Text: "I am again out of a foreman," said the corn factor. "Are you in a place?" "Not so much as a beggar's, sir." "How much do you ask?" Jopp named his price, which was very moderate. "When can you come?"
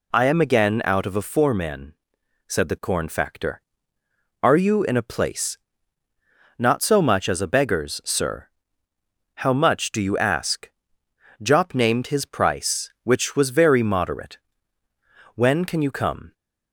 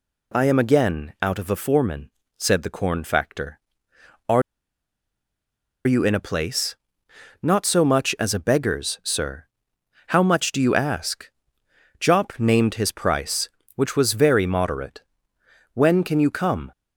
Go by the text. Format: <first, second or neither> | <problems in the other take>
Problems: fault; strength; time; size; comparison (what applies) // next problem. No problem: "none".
first | pauses between "Are" and "you"; strong; at 4.4 s; 1.4 s long